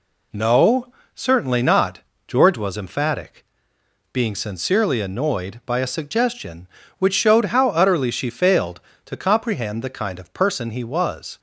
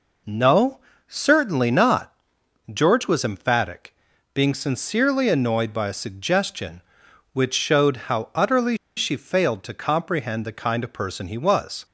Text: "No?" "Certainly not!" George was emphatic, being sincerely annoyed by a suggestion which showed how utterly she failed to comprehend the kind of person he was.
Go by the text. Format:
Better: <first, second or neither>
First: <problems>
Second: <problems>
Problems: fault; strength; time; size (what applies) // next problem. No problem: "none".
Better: first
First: none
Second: pauses between "utterly" and "she"; slight; at 8.7 s; 0.19 s long